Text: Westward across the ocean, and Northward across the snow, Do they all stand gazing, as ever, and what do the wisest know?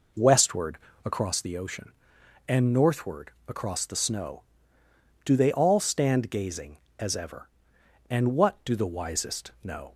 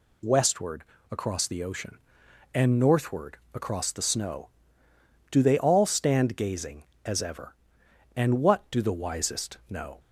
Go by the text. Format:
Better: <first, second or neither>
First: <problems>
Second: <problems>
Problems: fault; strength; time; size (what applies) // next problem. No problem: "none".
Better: second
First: starts louder than the rest; noticeable; until 1.3 s; 4.5 dB // pauses between "Westward" and "across"; slight; at 0.7 s; 0.28 s long // pauses between "Northward" and "across"; slight; at 3.3 s; 0.16 s long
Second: pauses between "Westward" and "across"; slight; at 0.8 s; 0.28 s long // pauses between "Northward" and "across"; slight; at 3.3 s; 0.16 s long